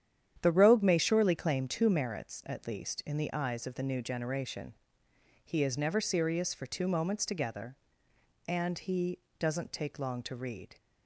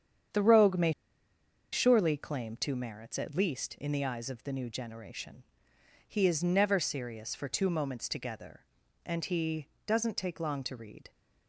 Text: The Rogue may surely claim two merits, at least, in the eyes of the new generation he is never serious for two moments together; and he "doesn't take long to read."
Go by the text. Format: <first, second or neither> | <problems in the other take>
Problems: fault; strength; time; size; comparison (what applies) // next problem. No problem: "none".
first | starts louder than the rest; strong; until 2.1 s; 8.5 dB; strong in the first // pauses between "may" and "surely"; noticeable; at 0.9 s; 0.79 s long // pauses between "generation" and "he"; noticeable; at 5.4 s; 0.62 s long; noticeable in the first // pauses between "he" and "doesn't"; slight; at 9.6 s; 0.18 s long; slight in the first